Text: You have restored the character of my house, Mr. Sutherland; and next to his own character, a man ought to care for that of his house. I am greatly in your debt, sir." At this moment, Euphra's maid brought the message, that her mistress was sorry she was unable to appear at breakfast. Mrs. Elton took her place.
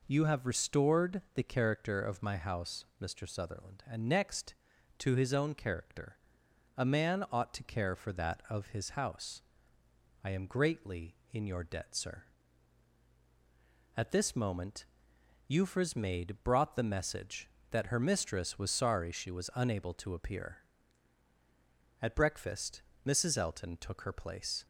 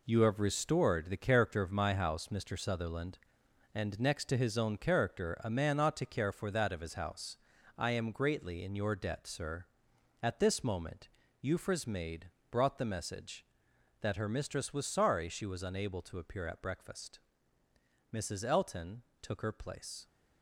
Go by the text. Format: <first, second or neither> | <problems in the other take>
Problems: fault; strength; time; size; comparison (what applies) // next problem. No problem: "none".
first | gets quieter; strong; throughout; 8.5 dB // pauses between "maid" and "brought"; slight; at 12.3 s; 0.20 s long // pauses between "Elton" and "took"; slight; at 19.0 s; 0.18 s long